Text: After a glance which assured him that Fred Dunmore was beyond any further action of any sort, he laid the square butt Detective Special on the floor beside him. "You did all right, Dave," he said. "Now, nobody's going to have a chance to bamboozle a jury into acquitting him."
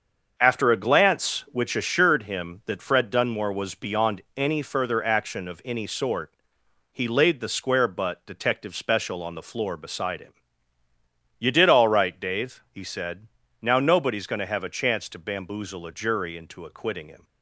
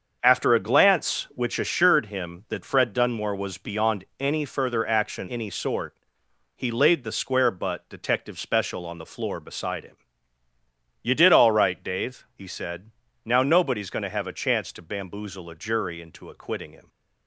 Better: first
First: starts louder than the rest; until 1.3 s; 6.5 dB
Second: starts louder than the rest; until 1.2 s; 6.5 dB // skips "of"; at 5.2 s

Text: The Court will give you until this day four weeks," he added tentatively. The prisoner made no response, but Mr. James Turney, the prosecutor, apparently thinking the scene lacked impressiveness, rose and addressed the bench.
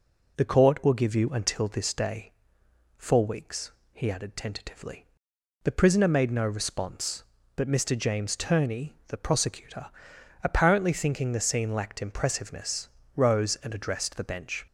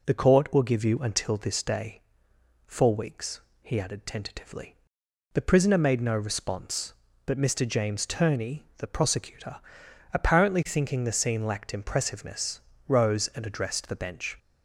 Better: neither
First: pauses between "day" and "four"; noticeable; at 2.3 s; 0.64 s long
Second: pauses between "day" and "four"; noticeable; at 2.0 s; 0.64 s long

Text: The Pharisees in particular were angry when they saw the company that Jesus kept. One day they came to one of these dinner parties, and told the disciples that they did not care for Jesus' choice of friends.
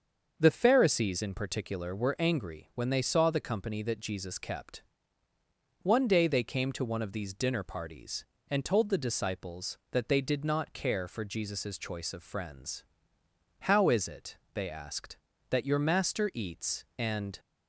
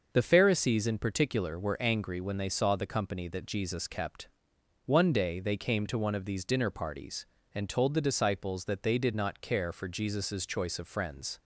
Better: second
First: starts louder than the rest; until 1.3 s; 6.5 dB // goes on to say "How is it they asked that your master eats and"; strong; from 13.6 s on; 3.7 s long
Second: starts louder than the rest; noticeable; until 1.1 s; 6 dB

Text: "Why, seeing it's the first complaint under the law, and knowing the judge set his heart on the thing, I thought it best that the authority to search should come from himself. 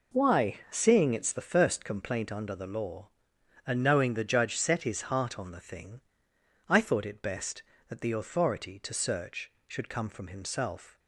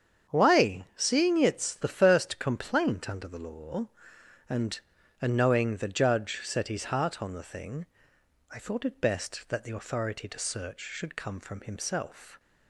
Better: first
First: none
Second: starts louder than the rest; strong; until 1.3 s; 7.5 dB // says "and" twice; at 5.2 s

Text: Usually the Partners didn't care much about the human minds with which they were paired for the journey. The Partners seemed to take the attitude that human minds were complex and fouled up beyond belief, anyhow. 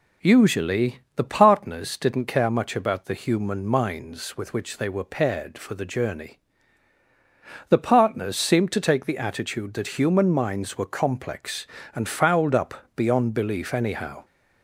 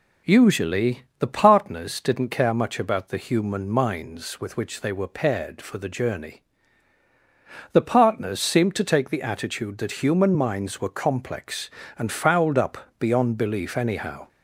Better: neither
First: pauses between "Usually" and "the"; slight; at 0.9 s; 0.16 s long // pauses between "up" and "beyond"; slight; at 12.7 s; 0.22 s long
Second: pauses between "Usually" and "the"; slight; at 1.0 s; 0.16 s long // pauses between "up" and "beyond"; slight; at 12.7 s; 0.22 s long

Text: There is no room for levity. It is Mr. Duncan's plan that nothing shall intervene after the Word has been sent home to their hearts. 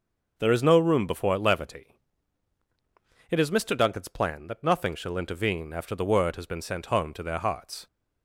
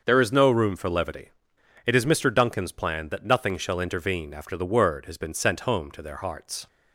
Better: second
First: starts louder than the rest; noticeable; until 1.3 s; 6 dB // says "before" for "for"; at 1.0 s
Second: starts louder than the rest; until 1.0 s; 6 dB

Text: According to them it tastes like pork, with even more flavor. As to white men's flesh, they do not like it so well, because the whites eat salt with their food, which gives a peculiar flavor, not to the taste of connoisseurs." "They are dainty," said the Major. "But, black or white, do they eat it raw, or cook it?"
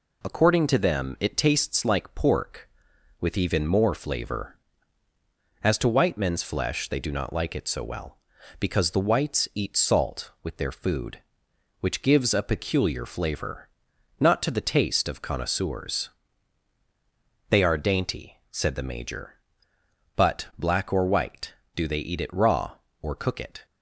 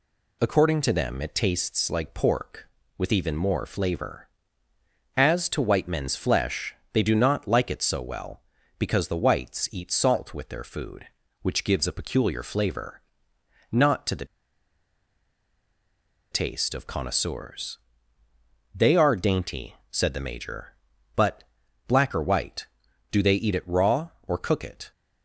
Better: first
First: none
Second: pauses between "the" and "taste"; strong; at 14.2 s; 2.0 s long

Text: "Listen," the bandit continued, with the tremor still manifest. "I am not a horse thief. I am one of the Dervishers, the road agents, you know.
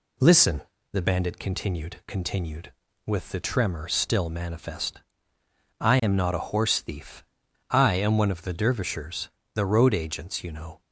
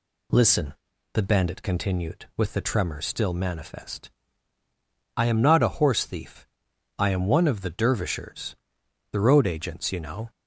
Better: second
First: says "continued" twice; at 2.0 s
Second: none

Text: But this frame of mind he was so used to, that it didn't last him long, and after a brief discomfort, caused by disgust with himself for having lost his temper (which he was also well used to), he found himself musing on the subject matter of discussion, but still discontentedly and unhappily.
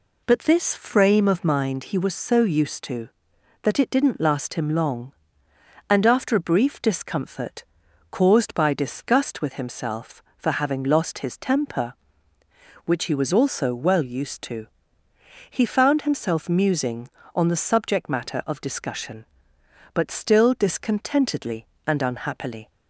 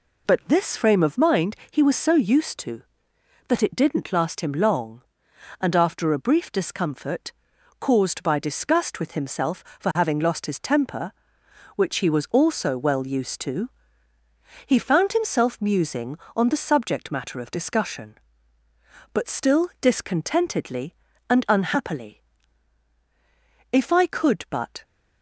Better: first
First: none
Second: goes on to say "If I could but"; noticeable; from 23.7 s on; 1.1 s long

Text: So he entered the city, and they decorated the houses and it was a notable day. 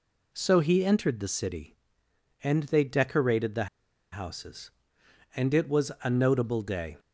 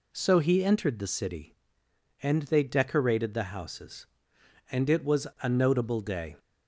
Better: second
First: pauses between "the" and "houses"; noticeable; at 3.6 s; 0.46 s long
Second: none

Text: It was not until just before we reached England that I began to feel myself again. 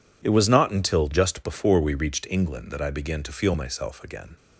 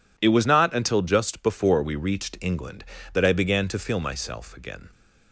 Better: neither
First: none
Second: none

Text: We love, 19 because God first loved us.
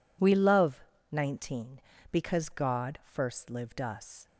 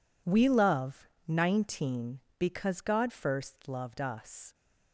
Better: second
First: says "lived" for "loved"; at 3.5 s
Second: none

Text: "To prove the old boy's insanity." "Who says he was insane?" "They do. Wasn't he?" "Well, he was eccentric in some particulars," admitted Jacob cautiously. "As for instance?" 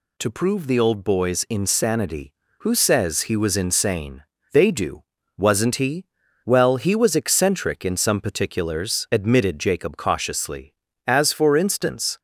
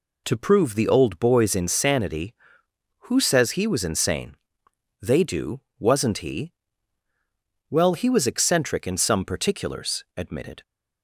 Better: first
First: none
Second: stops before "Jacob cautiously As for instance"; at 10.6 s

